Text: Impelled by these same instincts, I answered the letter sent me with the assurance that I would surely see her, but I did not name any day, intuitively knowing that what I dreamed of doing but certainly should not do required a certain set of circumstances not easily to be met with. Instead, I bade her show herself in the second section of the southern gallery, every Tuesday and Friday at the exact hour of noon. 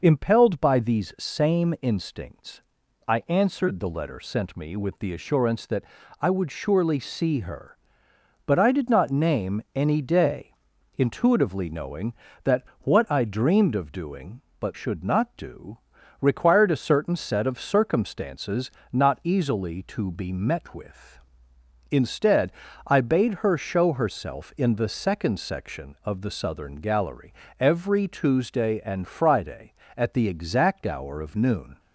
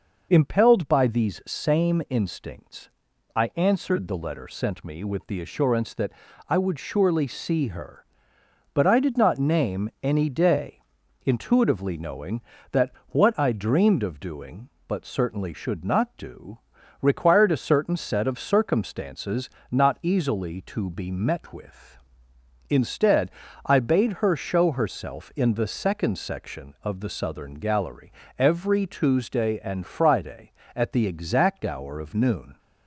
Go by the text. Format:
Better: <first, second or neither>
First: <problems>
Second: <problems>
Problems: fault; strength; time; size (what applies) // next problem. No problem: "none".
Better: second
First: pauses between "that" and "I"; slight; at 5.8 s; 0.36 s long // pauses between "that" and "what"; slight; at 12.6 s; 0.16 s long // skips "certainly"; at 14.7 s // pauses between "do" and "required"; at 15.7 s; 0.42 s long // pauses between "circumstances" and "not"; slight; at 18.6 s; 0.22 s long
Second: pauses between "that" and "I"; slight; at 6.1 s; 0.36 s long // pauses between "that" and "what"; slight; at 12.9 s; 0.16 s long // pauses between "do" and "required"; at 16.5 s; 0.42 s long // pauses between "circumstances" and "not"; slight; at 19.4 s; 0.22 s long